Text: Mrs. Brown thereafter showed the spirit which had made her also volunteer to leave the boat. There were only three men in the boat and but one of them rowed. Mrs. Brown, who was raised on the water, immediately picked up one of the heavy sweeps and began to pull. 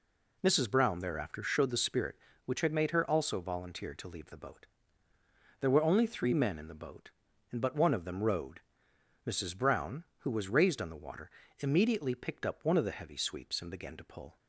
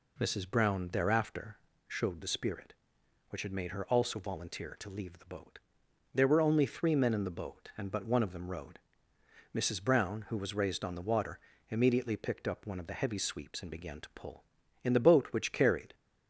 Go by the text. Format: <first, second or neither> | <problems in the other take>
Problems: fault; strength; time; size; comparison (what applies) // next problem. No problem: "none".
first | pauses between "thereafter" and "showed"; slight; at 1.5 s; 0.30 s long // goes on to say "In the boat which carried"; noticeable; from 14.8 s on; 1.1 s long